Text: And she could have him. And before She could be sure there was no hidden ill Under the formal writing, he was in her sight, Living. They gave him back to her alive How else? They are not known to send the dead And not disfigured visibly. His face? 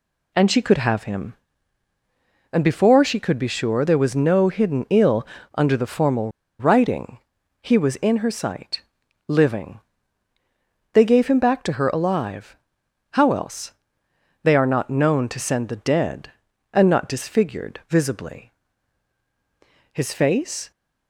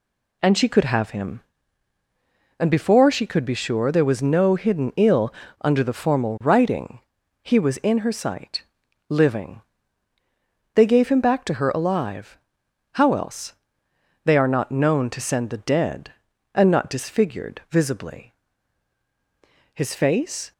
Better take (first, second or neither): second